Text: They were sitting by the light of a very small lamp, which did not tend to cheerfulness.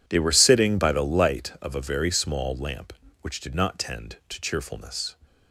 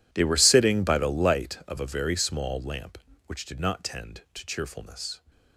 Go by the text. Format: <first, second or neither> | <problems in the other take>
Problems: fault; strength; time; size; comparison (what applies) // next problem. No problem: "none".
first | gets quieter; strong; throughout; 18.5 dB